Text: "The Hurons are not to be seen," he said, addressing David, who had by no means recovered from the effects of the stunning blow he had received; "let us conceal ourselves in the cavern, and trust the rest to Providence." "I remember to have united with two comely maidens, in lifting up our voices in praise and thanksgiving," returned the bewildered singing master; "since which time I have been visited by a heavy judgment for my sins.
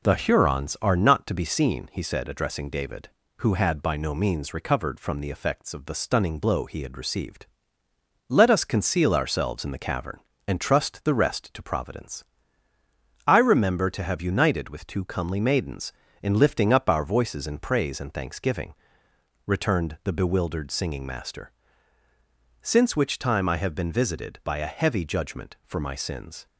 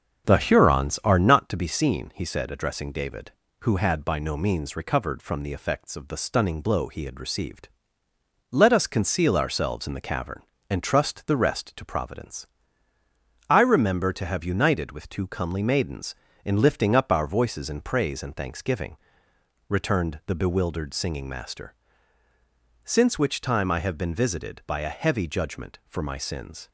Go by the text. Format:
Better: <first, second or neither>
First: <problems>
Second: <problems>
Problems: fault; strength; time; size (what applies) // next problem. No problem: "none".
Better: first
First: none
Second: starts louder than the rest; strong; until 1.5 s; 7.5 dB